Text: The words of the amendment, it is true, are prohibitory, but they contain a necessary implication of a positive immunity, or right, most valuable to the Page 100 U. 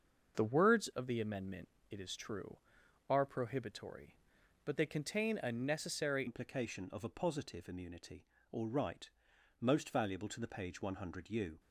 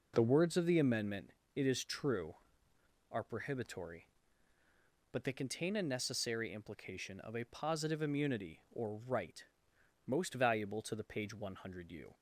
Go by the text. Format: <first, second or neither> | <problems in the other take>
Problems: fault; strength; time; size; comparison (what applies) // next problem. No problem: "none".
second | starts louder than the rest; until 1.3 s; 6.5 dB // changes voice at "implication"; from 6.2 s on; 5.3 s long